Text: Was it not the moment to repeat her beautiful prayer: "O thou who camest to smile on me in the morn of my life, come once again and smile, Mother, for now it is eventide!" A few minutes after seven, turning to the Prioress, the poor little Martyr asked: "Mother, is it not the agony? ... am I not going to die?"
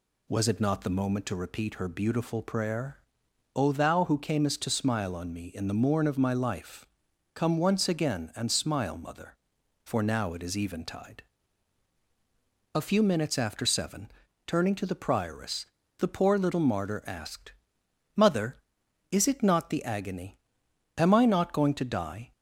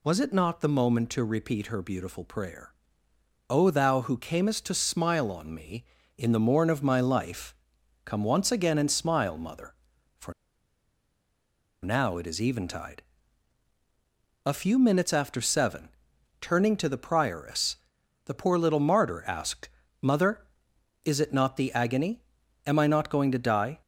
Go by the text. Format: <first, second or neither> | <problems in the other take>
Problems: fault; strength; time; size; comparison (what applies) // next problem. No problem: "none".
first | pauses between "for" and "now"; strong; at 10.3 s; 1.5 s long